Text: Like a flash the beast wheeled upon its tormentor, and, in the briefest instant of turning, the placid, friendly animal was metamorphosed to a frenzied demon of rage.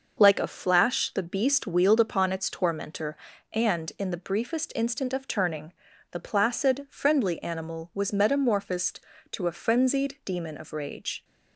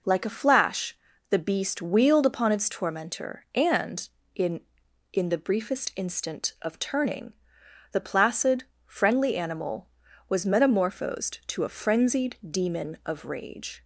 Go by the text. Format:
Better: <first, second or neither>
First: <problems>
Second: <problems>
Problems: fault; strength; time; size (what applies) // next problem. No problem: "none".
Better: first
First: none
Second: pauses between "flash" and "the"; slight; at 0.9 s; 0.34 s long // says "in" twice; at 5.1 s